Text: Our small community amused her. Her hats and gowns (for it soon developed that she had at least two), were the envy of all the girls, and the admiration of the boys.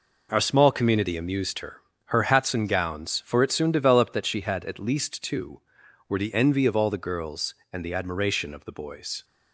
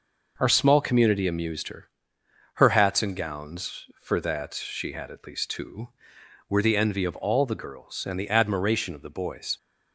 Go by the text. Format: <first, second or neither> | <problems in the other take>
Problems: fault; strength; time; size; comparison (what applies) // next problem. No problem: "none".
first | skips "it soon developed"; at 4.2 s